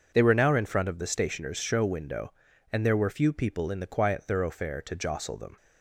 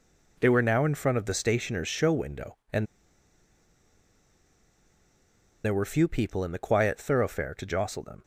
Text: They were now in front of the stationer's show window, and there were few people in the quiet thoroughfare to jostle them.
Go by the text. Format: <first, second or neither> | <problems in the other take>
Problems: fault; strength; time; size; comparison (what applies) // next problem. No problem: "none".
first | pauses between "and" and "there"; strong; at 2.8 s; 2.7 s long